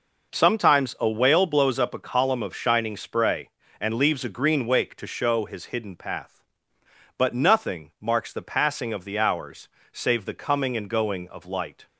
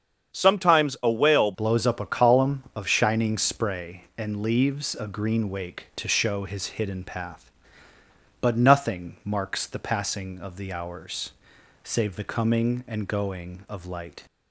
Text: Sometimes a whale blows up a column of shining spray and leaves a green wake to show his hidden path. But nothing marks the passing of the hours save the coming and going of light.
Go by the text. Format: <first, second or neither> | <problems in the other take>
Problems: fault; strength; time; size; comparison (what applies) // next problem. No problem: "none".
first | starts louder than the rest; strong; until 1.4 s; 7.5 dB // changes voice at "blows"; from 1.5 s on; 12.7 s long // pauses between "hours" and "save"; noticeable; at 11.3 s; 0.52 s long; slight in the first